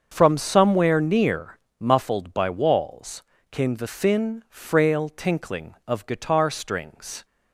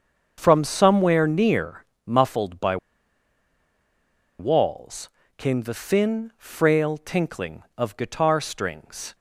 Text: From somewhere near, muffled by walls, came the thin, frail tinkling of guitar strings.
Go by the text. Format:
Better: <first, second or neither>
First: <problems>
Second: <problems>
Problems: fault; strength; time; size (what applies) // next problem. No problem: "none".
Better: first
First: starts louder than the rest; until 1.1 s; 7 dB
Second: starts louder than the rest; until 1.3 s; 7 dB // pauses between "by" and "walls"; strong; at 2.7 s; 1.6 s long